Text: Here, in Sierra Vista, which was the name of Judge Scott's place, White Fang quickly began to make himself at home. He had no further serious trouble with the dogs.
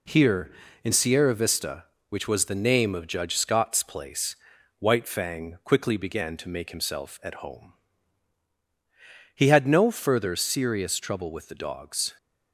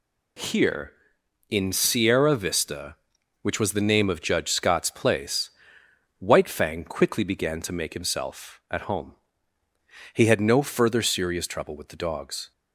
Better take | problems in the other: neither | none

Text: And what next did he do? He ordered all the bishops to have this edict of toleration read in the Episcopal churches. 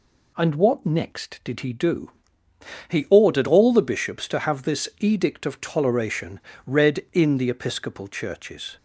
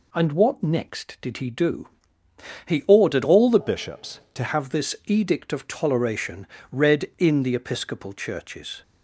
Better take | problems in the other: first | changes voice from "bishops" to "to"; from 3.5 to 4.4 s; 0.9 s long // pauses between "toleration" and "read"; slight; at 6.4 s; 0.24 s long; slight in the first

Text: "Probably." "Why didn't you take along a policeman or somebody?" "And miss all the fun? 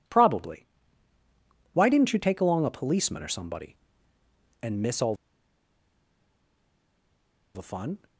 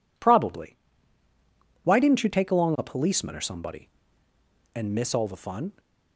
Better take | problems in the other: second | pauses between "all" and "the"; strong; at 5.1 s; 2.3 s long

